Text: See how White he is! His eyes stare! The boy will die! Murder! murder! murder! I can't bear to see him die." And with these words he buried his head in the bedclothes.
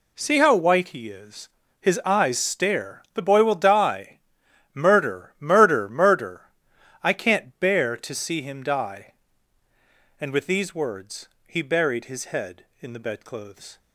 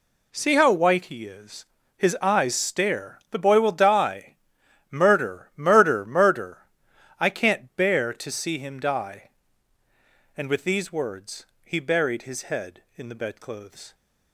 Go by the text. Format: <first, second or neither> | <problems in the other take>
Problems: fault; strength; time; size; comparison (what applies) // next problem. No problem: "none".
neither | pauses between "words" and "he"; slight; the same in both